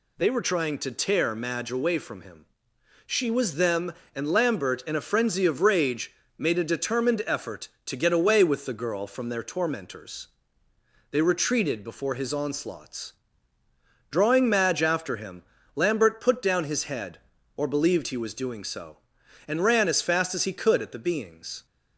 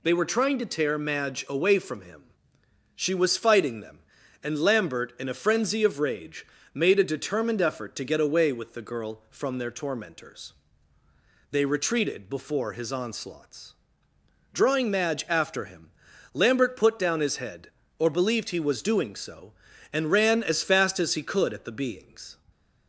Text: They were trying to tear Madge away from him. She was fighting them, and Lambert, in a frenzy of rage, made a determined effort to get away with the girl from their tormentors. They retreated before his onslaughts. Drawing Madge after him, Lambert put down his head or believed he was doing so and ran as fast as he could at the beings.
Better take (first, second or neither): second